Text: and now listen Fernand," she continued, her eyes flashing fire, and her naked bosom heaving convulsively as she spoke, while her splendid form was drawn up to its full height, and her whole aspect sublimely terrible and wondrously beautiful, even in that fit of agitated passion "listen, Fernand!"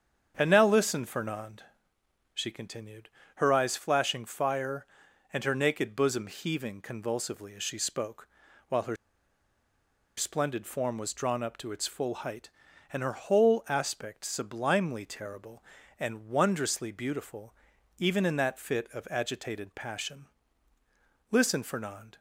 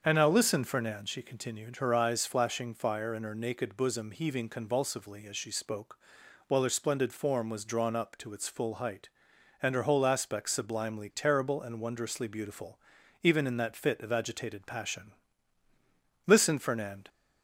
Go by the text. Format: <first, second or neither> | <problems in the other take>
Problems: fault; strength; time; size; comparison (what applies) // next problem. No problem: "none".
second | starts louder than the rest; strong; until 1.3 s; 7.5 dB; also in the second // pauses between "her" and "splendid"; at 8.9 s; 1.2 s long // pauses between "passion" and "listen"; at 20.2 s; 1.0 s long; also in the second